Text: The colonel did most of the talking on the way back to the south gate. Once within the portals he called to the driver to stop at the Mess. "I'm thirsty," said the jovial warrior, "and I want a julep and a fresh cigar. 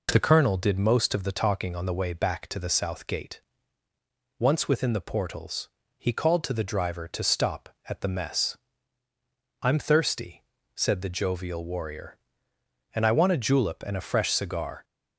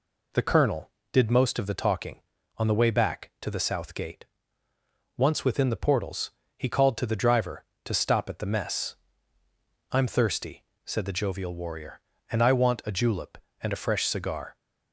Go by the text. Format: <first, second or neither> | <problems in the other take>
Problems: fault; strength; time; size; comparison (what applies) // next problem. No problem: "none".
neither | pauses between "portals" and "he"; slight; the same in both